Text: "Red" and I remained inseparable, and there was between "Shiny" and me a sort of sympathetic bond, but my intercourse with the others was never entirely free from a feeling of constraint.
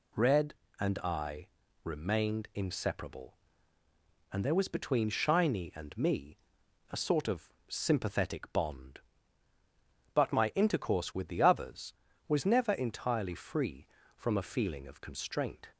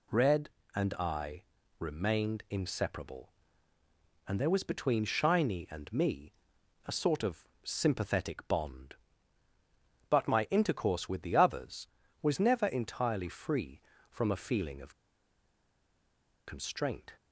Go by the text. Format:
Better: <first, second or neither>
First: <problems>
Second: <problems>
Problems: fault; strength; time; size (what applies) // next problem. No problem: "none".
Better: first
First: pauses between "I" and "remained"; slight; at 1.4 s; 0.34 s long // pauses between "me" and "a"; noticeable; at 6.3 s; 0.54 s long // pauses between "of" and "sympathetic"; slight; at 7.4 s; 0.18 s long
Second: pauses between "I" and "remained"; slight; at 1.4 s; 0.34 s long // pauses between "me" and "a"; noticeable; at 6.3 s; 0.54 s long // pauses between "of" and "sympathetic"; slight; at 7.4 s; 0.18 s long // pauses between "of" and "constraint"; strong; at 14.9 s; 1.5 s long